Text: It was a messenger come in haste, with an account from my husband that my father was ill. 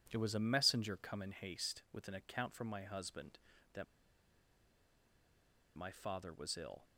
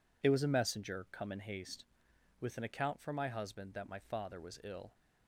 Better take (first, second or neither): second